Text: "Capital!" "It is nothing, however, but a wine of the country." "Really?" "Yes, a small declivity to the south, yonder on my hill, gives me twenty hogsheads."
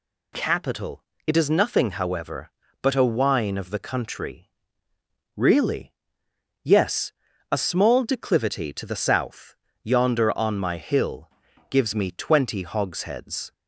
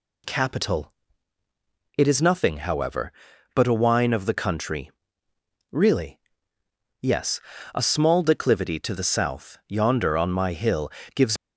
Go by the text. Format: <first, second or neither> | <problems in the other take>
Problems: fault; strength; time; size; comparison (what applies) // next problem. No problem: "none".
first | stops before "me twenty hogsheads"; at 11.3 s